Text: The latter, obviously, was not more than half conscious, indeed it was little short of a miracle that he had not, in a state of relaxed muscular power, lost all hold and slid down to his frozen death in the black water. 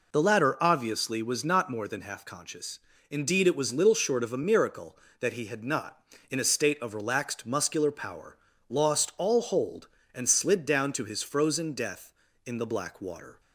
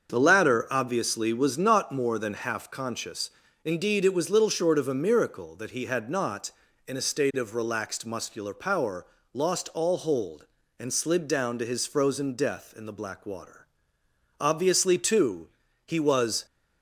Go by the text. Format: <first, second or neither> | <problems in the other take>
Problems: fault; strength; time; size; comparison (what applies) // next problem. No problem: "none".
first | starts louder than the rest; until 1.1 s; 6.5 dB // goes on to say "Obviously too he was"; strong; from 14.3 s on; 2.0 s long